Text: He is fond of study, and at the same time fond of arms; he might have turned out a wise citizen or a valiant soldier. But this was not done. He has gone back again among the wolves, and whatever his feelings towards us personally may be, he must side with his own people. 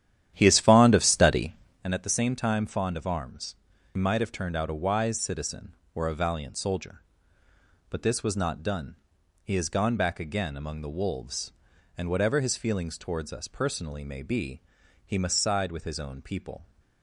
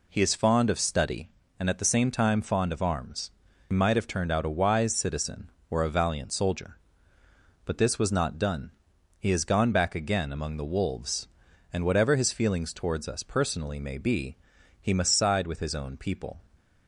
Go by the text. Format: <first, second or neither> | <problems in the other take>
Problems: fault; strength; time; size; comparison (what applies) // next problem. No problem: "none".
second | starts louder than the rest; strong; until 1.9 s; 11 dB